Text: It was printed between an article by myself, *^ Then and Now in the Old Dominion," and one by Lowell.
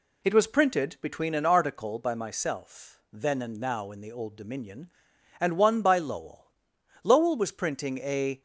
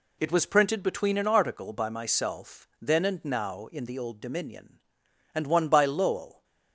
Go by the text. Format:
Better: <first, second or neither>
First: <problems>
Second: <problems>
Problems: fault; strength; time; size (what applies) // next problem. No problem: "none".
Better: second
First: goes on to say "Lowell was printing a"; from 7.0 s on; 1.3 s long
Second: none